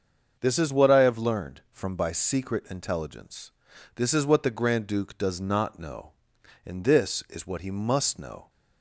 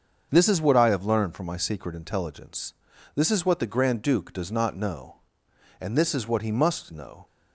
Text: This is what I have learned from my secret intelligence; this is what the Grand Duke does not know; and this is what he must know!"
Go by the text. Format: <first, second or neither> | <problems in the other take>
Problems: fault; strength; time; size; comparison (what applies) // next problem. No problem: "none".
second | starts louder than the rest; until 1.4 s; 6.5 dB; also in the second // says "by" for "my"; at 1.9 s